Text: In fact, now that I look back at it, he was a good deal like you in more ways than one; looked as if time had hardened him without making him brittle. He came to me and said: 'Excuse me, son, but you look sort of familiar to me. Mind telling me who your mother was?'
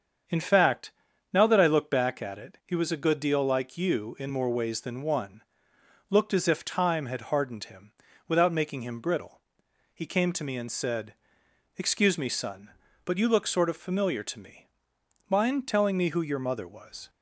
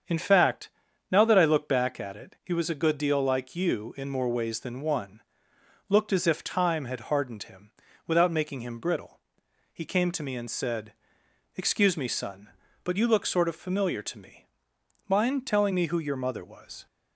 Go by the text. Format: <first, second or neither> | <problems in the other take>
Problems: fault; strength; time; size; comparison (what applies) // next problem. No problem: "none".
neither | starts louder than the rest; strong; the same in both // pauses between "him" and "without"; slight; the same in both